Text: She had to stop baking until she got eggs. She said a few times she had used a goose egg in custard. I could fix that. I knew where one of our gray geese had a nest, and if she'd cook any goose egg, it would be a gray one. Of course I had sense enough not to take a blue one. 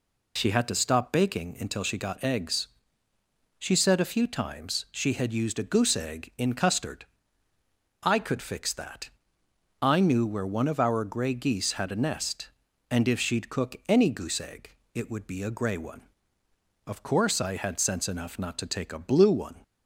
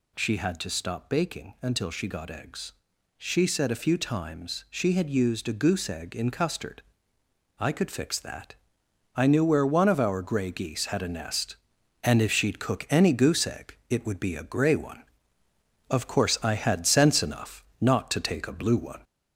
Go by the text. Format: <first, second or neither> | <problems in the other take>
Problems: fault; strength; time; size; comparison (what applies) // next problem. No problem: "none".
first | gets louder; slight; throughout; 2.5 dB // pauses between "enough" and "not"; slight; at 17.6 s; 0.16 s long